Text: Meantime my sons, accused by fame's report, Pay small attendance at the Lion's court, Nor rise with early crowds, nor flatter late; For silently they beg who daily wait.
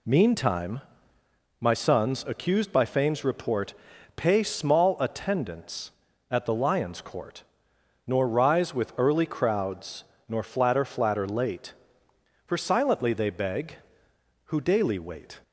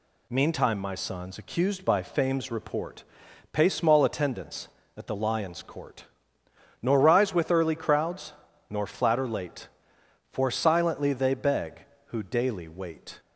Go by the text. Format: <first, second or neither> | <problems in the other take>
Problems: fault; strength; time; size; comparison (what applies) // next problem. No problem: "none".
second | pauses between "Meantime" and "my"; noticeable; at 0.8 s; 0.78 s long // says "flatter" twice; at 10.8 s